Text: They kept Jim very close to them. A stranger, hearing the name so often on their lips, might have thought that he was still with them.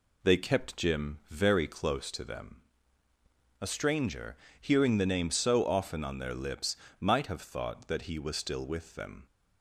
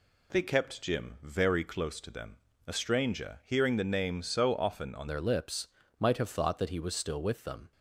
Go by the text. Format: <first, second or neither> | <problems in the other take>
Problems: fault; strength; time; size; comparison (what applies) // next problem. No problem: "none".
first | changes voice at "their"; from 5.0 s on; 2.7 s long